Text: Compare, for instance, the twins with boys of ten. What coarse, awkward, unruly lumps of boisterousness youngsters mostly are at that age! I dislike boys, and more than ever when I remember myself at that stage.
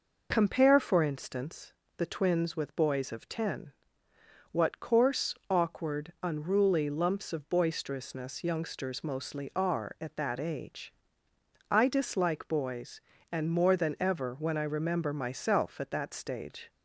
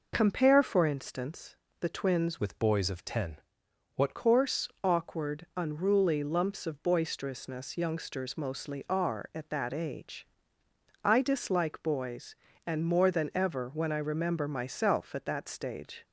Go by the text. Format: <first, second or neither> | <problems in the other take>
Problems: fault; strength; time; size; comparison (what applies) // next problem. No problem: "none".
first | changes voice from "with" to "What"; from 2.3 to 4.1 s; 1.8 s long